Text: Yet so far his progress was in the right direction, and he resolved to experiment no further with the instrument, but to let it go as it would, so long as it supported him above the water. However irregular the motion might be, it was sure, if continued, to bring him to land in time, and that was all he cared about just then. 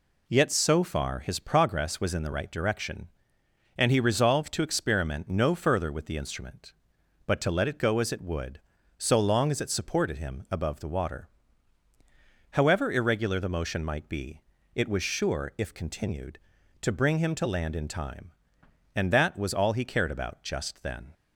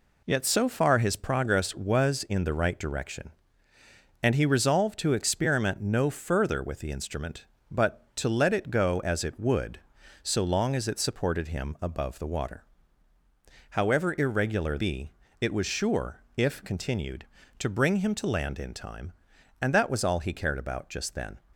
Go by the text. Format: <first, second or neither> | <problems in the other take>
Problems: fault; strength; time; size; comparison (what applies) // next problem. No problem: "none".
first | skips "the motion might"; at 14.7 s